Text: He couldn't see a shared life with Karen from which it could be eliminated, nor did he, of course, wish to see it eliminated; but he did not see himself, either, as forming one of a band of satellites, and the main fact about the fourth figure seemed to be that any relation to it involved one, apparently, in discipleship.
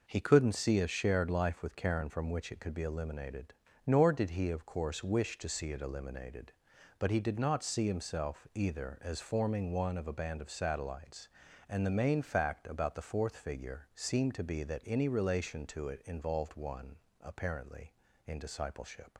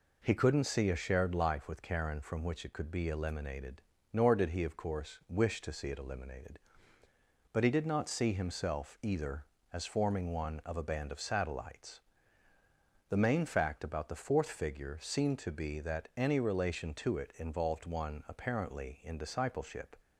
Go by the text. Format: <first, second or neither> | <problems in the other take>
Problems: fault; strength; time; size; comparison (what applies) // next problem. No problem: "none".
first | skips "and"; at 12.5 s